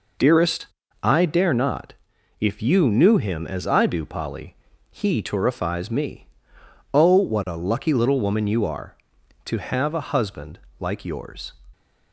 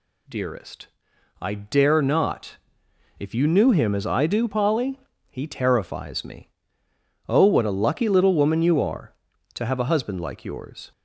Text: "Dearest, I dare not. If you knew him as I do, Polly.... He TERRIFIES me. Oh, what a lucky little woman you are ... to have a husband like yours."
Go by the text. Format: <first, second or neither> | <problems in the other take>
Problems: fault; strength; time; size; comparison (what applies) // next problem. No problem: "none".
second | gets quieter; strong; throughout; 7.5 dB // pauses between "husband" and "like"; slight; at 10.5 s; 0.18 s long